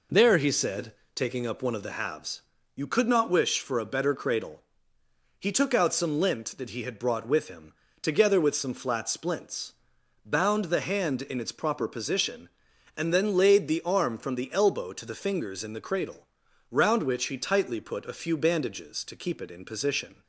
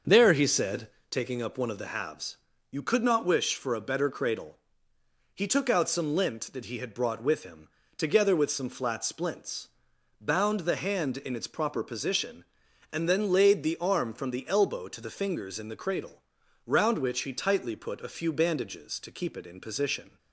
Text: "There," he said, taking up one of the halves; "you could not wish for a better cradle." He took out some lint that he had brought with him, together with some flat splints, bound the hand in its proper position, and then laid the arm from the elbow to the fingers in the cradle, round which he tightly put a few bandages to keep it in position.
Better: first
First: none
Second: starts louder than the rest; until 1.2 s; 6.5 dB

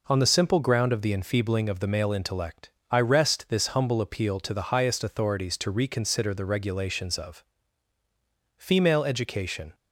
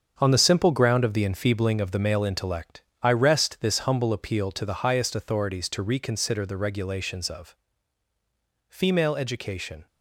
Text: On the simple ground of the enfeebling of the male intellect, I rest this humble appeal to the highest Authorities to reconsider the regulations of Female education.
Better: first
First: pauses between "of" and "Female"; at 7.4 s; 1.1 s long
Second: gets quieter; strong; throughout; 8.5 dB // pauses between "of" and "Female"; at 7.5 s; 1.1 s long

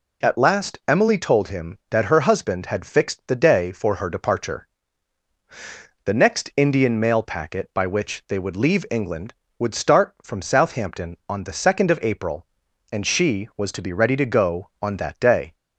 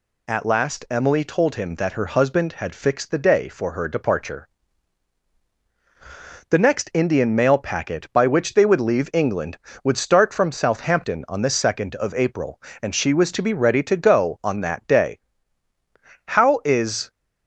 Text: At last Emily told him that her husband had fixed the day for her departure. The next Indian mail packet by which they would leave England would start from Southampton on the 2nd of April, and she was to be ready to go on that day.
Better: first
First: none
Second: goes on to say "How is"; noticeable; from 16.2 s on; 0.82 s long

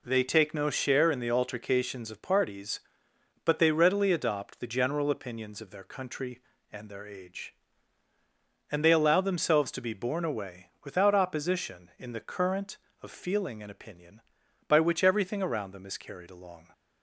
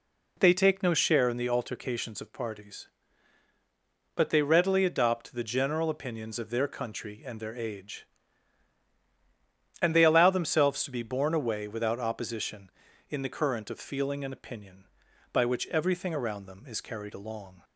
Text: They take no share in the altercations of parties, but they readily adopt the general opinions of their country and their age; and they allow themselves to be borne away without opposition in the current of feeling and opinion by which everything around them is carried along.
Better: neither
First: none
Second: none

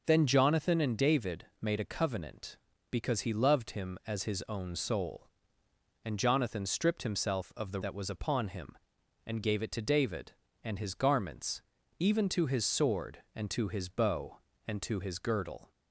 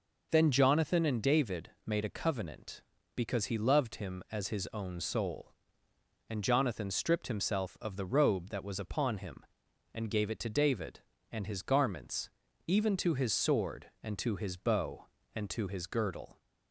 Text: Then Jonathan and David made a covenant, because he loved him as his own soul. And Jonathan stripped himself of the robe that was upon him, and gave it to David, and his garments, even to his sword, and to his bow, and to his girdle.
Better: second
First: pauses between "David" and "made"; slight; at 1.4 s; 0.16 s long // skips "robe"; at 7.8 s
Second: pauses between "David" and "made"; slight; at 1.6 s; 0.16 s long

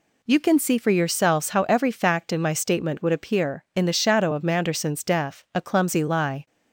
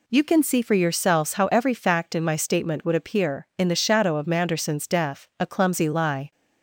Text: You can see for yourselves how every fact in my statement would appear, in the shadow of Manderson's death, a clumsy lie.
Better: neither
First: none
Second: none

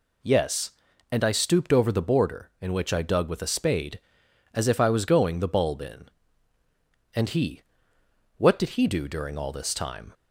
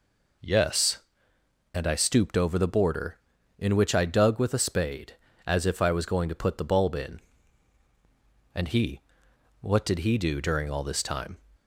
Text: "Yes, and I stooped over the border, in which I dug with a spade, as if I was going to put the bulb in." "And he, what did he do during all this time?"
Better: second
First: skips "to put"; at 5.4 s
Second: none

